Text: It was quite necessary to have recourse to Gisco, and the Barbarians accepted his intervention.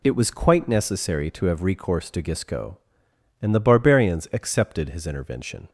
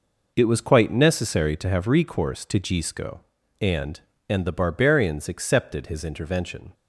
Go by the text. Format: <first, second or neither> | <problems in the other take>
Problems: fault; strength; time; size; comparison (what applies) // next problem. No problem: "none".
first | says "and" twice; at 4.3 s